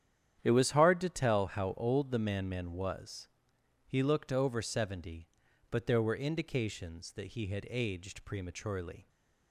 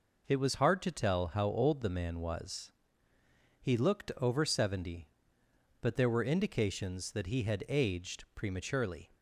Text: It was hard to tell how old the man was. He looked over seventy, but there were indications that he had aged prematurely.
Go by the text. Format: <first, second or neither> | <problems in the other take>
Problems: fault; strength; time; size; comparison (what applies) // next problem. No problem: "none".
second | starts louder than the rest; strong; until 1.4 s; 10 dB // says "man" twice; at 2.4 s